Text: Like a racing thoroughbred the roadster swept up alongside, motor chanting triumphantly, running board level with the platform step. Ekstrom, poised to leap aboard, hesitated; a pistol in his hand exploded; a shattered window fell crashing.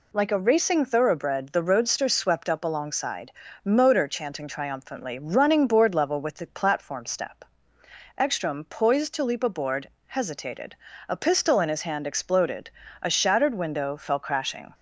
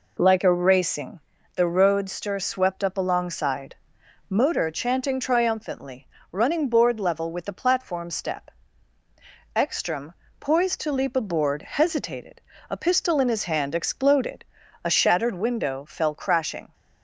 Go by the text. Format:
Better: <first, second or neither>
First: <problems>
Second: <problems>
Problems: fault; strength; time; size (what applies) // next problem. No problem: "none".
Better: first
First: none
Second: skips "thoroughbred"; at 1.3 s